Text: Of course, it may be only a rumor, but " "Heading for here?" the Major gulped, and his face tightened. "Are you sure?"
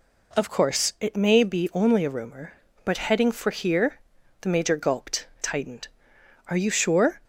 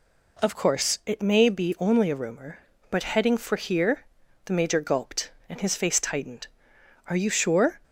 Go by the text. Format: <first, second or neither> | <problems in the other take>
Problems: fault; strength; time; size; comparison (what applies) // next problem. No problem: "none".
second | skips "and his face"; at 5.3 s